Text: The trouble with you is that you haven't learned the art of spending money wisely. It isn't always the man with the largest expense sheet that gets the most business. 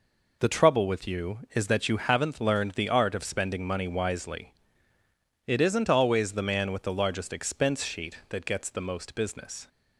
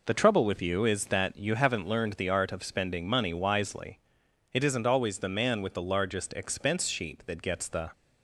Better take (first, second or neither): first